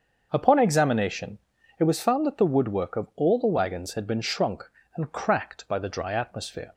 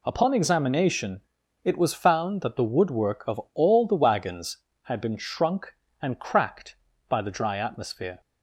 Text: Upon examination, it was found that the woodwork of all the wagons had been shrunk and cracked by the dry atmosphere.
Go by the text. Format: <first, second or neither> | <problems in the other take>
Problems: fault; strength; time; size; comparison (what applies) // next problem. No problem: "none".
second | starts louder than the rest; until 1.9 s; 6.5 dB